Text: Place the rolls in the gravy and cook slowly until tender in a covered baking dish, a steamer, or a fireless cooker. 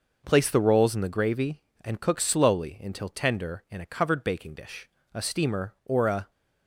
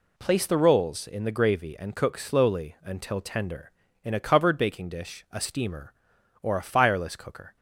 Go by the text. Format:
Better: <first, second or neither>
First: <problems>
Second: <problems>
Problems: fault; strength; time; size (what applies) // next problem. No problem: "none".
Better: second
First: stops before "fireless cooker"; at 6.3 s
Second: none